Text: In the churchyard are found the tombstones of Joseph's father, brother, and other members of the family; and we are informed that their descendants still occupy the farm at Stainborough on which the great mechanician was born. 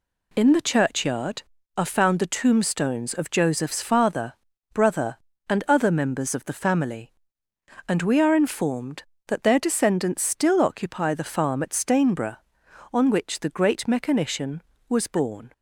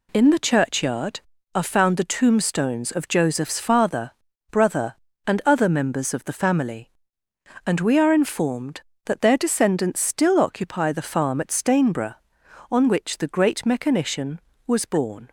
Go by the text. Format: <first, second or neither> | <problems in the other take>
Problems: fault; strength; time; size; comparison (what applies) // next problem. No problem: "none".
neither | none